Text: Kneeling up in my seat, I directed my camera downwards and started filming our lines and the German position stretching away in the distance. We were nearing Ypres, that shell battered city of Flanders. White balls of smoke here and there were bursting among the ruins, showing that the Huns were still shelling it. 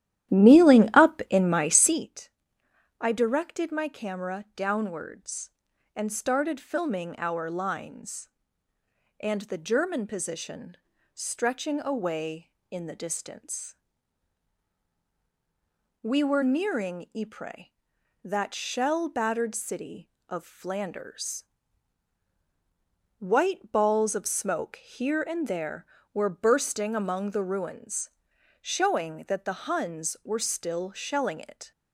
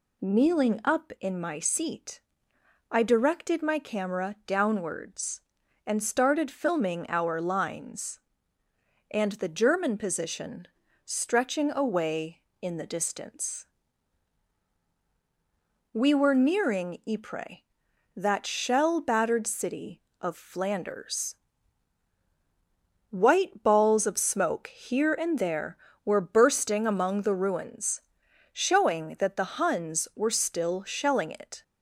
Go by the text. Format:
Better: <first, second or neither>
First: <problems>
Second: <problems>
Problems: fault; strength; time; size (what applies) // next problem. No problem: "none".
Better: second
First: starts louder than the rest; strong; until 2.1 s; 12.5 dB // pauses between "position" and "stretching"; at 10.7 s; 0.38 s long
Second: pauses between "position" and "stretching"; at 10.6 s; 0.38 s long